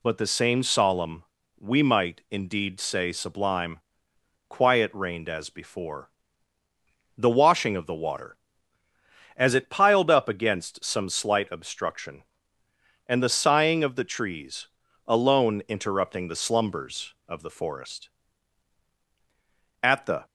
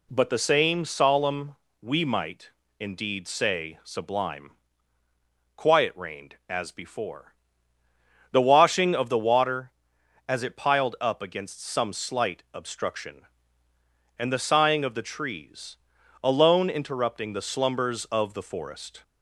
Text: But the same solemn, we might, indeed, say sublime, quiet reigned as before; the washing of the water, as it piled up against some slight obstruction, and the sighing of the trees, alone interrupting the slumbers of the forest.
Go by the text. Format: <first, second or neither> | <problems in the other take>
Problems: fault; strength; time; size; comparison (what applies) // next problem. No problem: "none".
second | goes on to say "At the"; slight; from 19.8 s on; 0.42 s long